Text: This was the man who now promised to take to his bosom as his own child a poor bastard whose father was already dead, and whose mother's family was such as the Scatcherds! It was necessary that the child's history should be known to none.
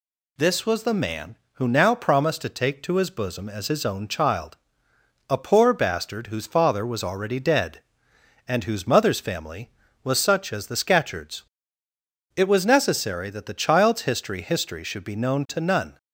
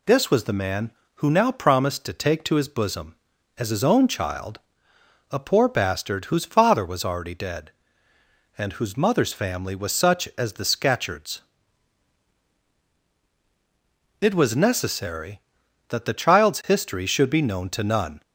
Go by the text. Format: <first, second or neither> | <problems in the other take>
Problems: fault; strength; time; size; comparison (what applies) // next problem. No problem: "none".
second | pauses between "child" and "a"; noticeable; at 4.5 s; 0.74 s long; noticeable in the second // says "history" twice; at 14.4 s